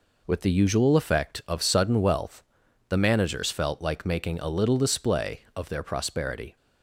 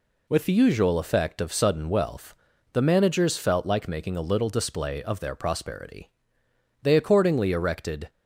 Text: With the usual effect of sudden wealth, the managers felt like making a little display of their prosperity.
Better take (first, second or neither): first